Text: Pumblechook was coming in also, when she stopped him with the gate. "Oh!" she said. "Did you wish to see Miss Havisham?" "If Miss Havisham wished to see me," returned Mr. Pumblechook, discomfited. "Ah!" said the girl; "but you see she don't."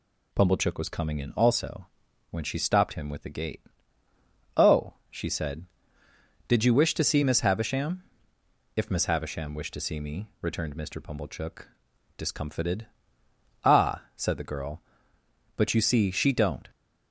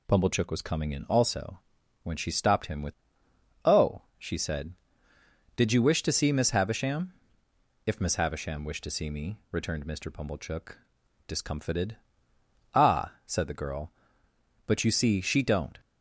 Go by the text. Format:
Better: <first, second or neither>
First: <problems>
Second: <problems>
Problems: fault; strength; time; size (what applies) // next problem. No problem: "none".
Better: first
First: none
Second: skips "the gate"; at 3.2 s